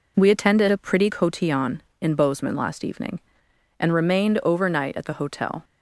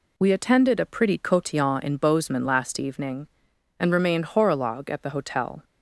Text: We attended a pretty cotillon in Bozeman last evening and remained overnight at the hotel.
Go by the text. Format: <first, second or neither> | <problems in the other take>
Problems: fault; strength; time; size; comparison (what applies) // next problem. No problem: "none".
first | says "horologue" for "overnight"; at 4.2 s